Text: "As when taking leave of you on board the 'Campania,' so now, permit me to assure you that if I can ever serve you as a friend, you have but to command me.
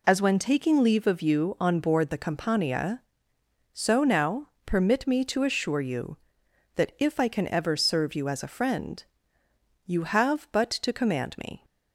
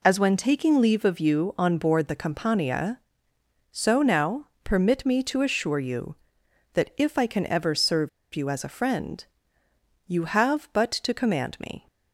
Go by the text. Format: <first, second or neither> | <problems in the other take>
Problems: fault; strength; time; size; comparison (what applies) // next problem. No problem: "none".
first | pauses between "serve" and "you"; slight; at 8.0 s; 0.25 s long